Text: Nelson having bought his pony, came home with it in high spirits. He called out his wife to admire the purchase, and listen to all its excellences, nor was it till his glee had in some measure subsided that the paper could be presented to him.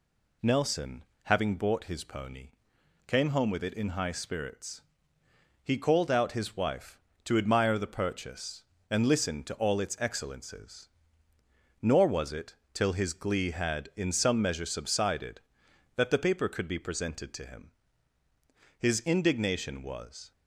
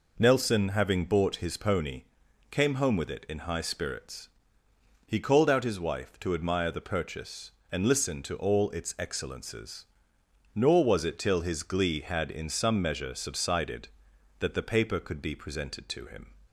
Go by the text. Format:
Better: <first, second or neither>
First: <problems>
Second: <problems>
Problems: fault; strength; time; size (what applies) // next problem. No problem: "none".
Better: second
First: pauses between "Nelson" and "having"; slight; at 1.0 s; 0.20 s long // pauses between "it" and "till"; slight; at 12.5 s; 0.18 s long // goes on to say "His indignation was"; from 18.7 s on; 1.5 s long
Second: none